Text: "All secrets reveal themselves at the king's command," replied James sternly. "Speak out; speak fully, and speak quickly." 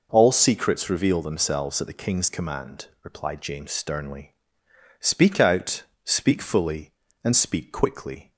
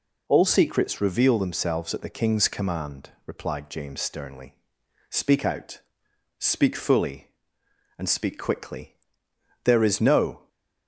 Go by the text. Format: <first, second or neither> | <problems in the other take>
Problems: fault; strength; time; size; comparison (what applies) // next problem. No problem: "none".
first | goes on to say "There is no"; noticeable; from 9.6 s on; 0.82 s long